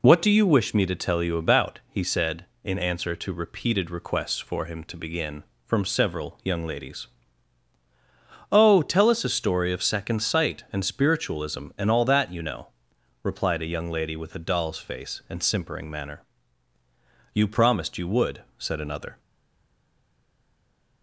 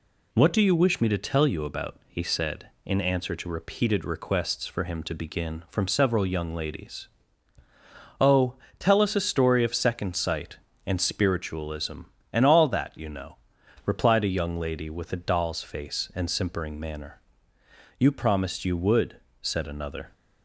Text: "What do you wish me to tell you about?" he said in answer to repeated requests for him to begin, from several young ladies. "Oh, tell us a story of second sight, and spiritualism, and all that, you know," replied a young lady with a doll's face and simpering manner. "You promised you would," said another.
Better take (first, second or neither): second